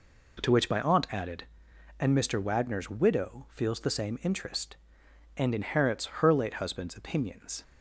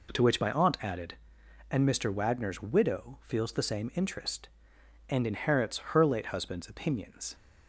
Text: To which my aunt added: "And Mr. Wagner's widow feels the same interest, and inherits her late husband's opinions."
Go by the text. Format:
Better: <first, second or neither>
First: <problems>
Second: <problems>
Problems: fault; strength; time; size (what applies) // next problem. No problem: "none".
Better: neither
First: pauses between "inherits" and "her"; slight; at 6.0 s; 0.16 s long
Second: pauses between "inherits" and "her"; slight; at 5.7 s; 0.16 s long